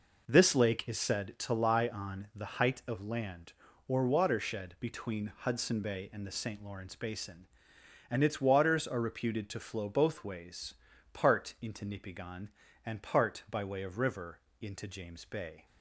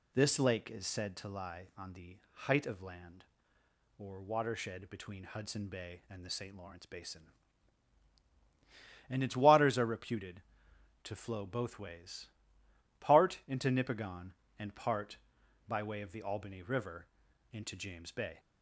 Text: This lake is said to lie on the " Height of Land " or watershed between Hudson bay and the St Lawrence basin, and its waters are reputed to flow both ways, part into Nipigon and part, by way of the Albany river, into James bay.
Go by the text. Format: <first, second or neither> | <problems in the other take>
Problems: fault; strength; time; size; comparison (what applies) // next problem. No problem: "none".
second | skips "the Albany"; at 13.9 s